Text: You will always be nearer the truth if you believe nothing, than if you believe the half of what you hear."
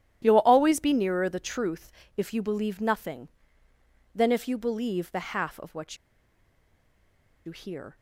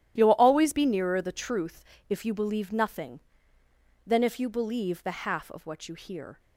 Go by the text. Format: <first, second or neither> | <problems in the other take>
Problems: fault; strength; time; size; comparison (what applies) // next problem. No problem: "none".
second | starts louder than the rest; strong; until 1.2 s; 12 dB; strong in the second // pauses between "truth" and "if"; slight; at 1.9 s; 0.24 s long; slight in the second // pauses between "what" and "you"; strong; at 5.9 s; 1.4 s long